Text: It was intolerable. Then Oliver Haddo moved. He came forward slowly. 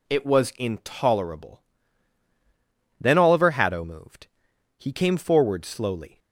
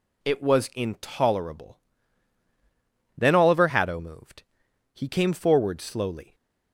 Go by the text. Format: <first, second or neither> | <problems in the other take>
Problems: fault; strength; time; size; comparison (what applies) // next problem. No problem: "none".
neither | none